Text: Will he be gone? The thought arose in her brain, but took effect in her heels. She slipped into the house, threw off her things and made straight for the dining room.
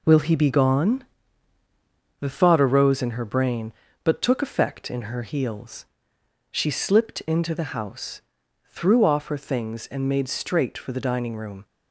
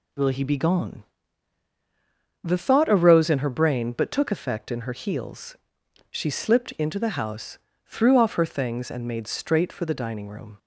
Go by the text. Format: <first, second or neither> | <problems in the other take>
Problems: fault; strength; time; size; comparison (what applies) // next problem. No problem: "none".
second | gets quieter; throughout; 6.5 dB